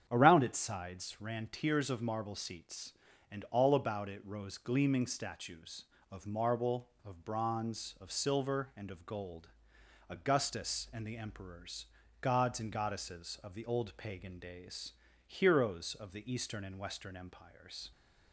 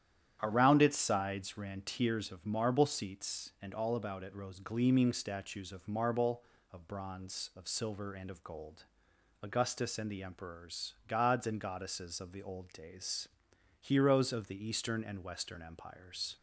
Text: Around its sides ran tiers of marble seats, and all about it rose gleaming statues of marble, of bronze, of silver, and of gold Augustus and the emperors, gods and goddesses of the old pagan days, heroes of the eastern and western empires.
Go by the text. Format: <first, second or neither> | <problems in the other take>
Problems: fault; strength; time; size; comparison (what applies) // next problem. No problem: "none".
first | starts louder than the rest; strong; until 1.4 s; 10 dB; strong in the first // pauses between "gold" and "Augustus"; noticeable; at 8.8 s; 0.58 s long; noticeable in the first // skips "pagan"; at 12.7 s